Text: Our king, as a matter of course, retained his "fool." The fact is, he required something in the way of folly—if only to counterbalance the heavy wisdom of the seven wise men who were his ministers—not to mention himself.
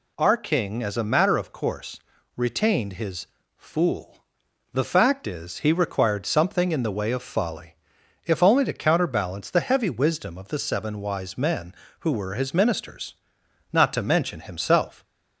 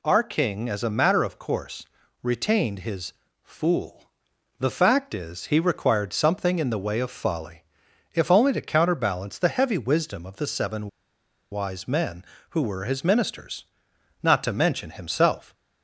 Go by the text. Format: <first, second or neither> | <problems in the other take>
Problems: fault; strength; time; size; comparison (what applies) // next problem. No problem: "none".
first | pauses between "his" and "fool"; slight; at 3.1 s; 0.30 s long; slight in the first // pauses between "seven" and "wise"; noticeable; at 10.8 s; 0.62 s long